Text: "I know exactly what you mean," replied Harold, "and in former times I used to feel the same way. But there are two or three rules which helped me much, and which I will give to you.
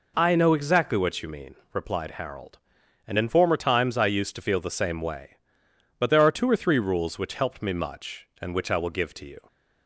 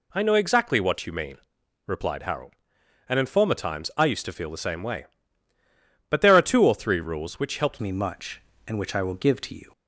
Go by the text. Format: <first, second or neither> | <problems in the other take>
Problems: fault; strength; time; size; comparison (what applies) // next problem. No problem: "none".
first | changes voice at "me"; from 7.7 s on; 2.0 s long